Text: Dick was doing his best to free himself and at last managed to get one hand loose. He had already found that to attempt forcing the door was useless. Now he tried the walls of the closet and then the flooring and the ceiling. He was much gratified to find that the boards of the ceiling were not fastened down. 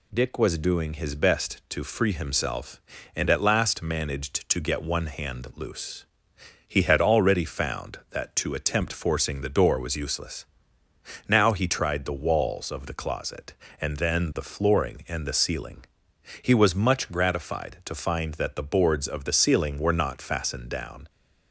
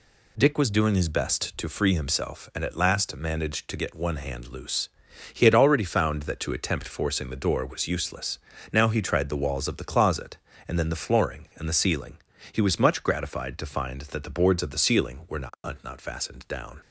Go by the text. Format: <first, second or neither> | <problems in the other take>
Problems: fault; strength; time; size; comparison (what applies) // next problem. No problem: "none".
first | says "not" twice; at 15.8 s